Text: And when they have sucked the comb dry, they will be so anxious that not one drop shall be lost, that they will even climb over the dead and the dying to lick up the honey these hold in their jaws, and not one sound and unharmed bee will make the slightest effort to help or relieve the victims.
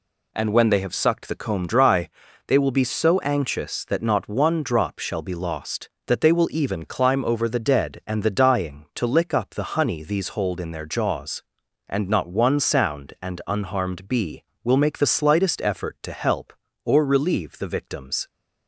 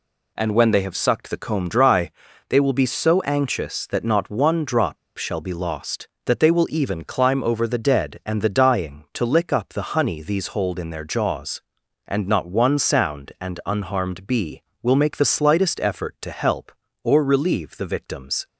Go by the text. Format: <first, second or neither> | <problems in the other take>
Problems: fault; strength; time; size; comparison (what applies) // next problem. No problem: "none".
first | pauses between "drop" and "shall"; slight; at 4.9 s; 0.20 s long